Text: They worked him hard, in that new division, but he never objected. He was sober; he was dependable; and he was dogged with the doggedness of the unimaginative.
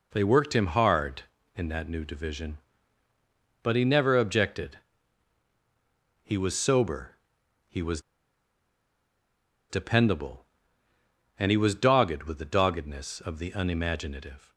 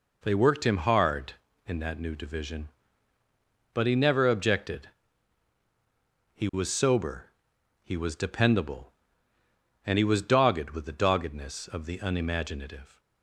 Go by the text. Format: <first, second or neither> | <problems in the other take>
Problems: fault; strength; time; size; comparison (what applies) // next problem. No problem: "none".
second | pauses between "was" and "dependable"; strong; at 8.0 s; 1.6 s long